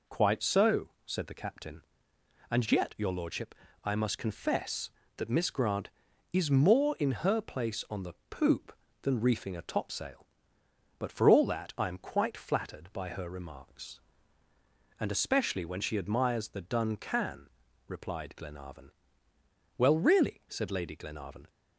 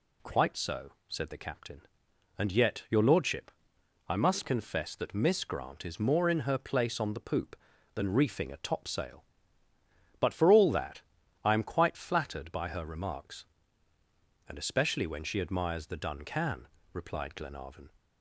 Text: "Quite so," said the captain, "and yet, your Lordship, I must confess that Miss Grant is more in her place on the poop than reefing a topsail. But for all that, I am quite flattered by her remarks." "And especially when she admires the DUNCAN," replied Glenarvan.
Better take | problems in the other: second | pauses between "the" and "poop"; slight; at 8.1 s; 0.16 s long // goes on to say "Well really said Lady Glenarvan"; strong; from 19.7 s on; 1.7 s long

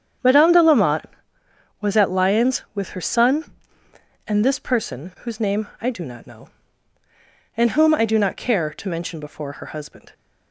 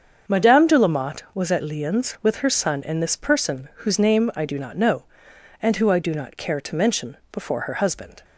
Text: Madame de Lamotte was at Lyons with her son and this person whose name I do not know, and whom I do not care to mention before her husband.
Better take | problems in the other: first | starts louder than the rest; until 1.3 s; 7 dB; strong in the first // says "who" for "whom"; at 5.7 s

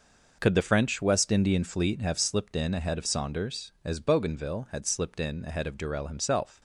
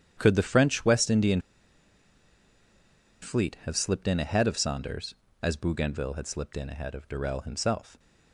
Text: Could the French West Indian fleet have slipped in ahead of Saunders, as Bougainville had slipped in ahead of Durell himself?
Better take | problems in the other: first | starts louder than the rest; strong; until 1.1 s; 9.5 dB // pauses between "Indian" and "fleet"; strong; at 1.4 s; 1.8 s long

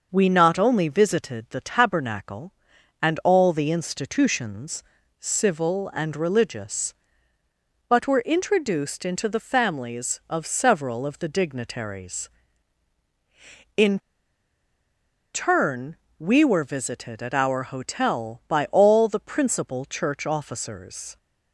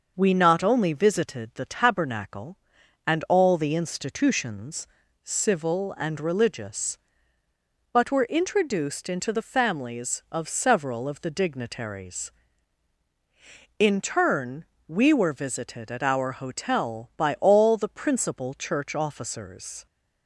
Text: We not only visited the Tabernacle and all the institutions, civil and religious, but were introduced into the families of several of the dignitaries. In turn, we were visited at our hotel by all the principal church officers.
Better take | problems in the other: second | starts louder than the rest; noticeable; until 1.1 s; 6 dB; noticeable in the second // pauses between "In" and "turn"; strong; at 13.9 s; 1.3 s long

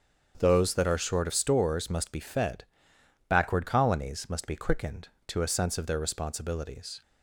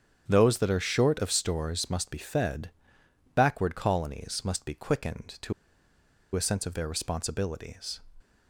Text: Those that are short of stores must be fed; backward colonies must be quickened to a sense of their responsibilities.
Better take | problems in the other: first | starts louder than the rest; strong; until 1.2 s; 8.5 dB; strong in the first // pauses between "to" and "a"; noticeable; at 5.5 s; 0.81 s long

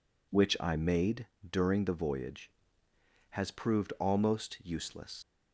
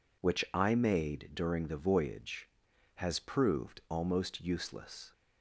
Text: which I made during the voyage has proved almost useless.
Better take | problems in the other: second | pauses between "made" and "during"; slight; at 1.2 s; 0.22 s long // leaves "useless" unfinished; at 5.2 s; 95 ms

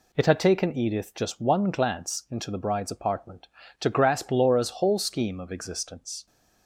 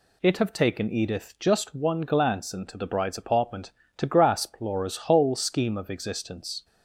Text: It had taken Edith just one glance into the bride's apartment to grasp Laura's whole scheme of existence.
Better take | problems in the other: first | says "have" for "had"; at 0.3 s

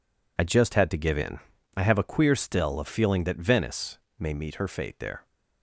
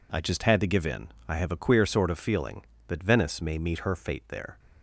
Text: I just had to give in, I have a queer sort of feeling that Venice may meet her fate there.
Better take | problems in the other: second | says "still" for "sort"; at 2.3 s // pauses between "Venice" and "may"; slight; at 3.9 s; 0.22 s long

